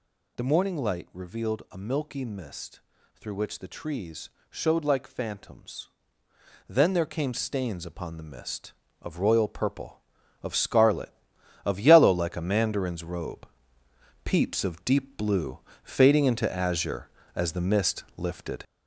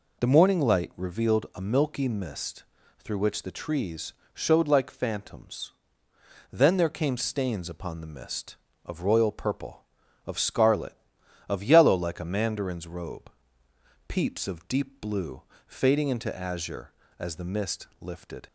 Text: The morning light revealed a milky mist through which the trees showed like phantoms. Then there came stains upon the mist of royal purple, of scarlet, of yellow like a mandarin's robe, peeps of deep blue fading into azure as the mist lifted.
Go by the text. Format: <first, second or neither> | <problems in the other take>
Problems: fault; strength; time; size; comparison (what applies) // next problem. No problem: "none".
second | gets louder; noticeable; throughout; 5 dB // pauses between "mist" and "through"; slight; at 2.7 s; 0.36 s long; slight in the second // pauses between "trees" and "showed"; slight; at 4.2 s; 0.20 s long; slight in the second // pauses between "blue" and "fading"; slight; at 15.5 s; 0.24 s long; slight in the second